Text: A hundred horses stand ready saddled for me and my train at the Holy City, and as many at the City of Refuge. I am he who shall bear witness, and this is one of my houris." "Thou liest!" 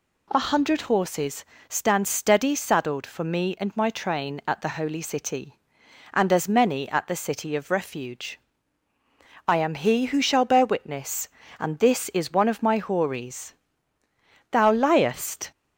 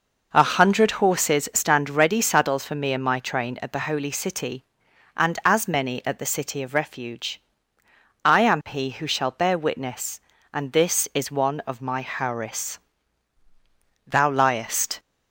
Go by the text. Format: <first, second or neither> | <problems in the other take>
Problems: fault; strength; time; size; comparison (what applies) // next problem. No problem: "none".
second | pauses between "horses" and "stand"; slight; at 1.4 s; 0.24 s long // says "steady" for "ready"; at 2.0 s